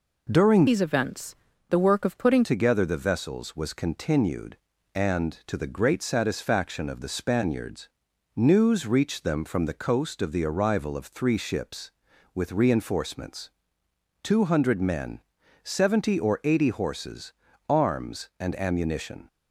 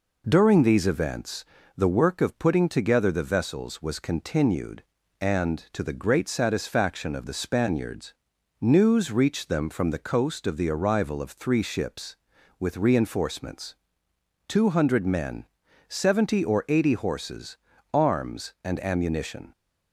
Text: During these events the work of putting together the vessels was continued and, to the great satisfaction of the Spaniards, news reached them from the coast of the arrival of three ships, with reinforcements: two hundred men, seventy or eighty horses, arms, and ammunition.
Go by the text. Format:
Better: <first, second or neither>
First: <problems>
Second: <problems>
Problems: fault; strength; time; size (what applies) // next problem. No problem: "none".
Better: second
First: changes voice from "these" to "putting"; from 0.6 to 2.4 s; 1.8 s long // pauses between "events" and "the"; slight; at 1.3 s; 0.34 s long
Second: pauses between "events" and "the"; slight; at 1.4 s; 0.32 s long